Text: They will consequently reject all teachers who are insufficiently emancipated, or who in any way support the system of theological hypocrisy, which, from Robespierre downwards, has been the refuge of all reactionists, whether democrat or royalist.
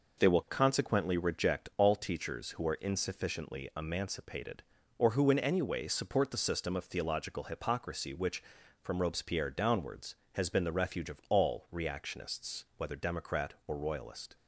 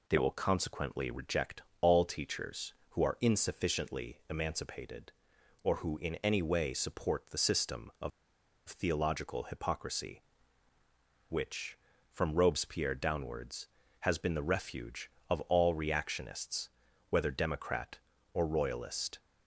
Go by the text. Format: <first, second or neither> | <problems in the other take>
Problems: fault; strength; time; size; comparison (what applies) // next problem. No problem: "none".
first | pauses between "reject" and "all"; slight; at 1.6 s; 0.20 s long // pauses between "of" and "theological"; noticeable; at 8.1 s; 0.59 s long